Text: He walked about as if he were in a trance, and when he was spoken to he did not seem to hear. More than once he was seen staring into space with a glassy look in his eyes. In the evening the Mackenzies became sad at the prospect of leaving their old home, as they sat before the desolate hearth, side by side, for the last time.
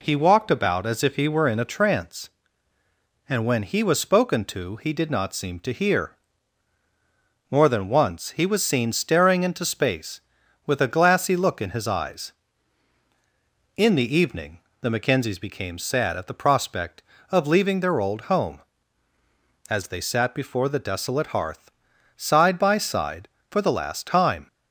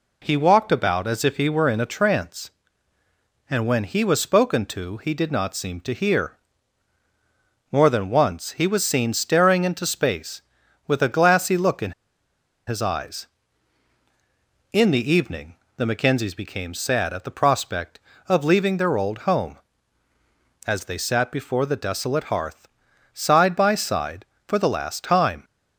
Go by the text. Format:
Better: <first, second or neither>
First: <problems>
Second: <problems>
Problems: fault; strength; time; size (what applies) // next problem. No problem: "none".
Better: first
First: pauses between "evening" and "the"; slight; at 14.6 s; 0.20 s long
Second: pauses between "in" and "his"; noticeable; at 11.9 s; 0.76 s long // pauses between "evening" and "the"; slight; at 15.5 s; 0.20 s long